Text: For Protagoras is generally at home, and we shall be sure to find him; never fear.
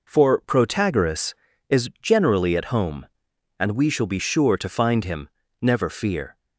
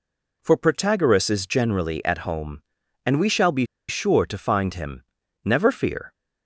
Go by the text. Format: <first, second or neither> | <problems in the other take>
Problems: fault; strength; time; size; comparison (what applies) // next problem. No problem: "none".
first | pauses between "be" and "sure"; slight; at 3.6 s; 0.23 s long